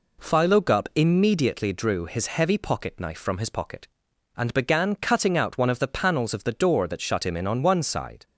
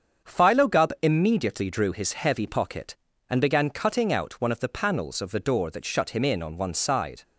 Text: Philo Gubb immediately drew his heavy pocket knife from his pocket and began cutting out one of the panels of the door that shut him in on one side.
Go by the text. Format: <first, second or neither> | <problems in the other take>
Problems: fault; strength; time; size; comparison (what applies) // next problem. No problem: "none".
first | starts louder than the rest; strong; until 1.3 s; 7.5 dB // skips "knife from his pocket"; at 3.1 s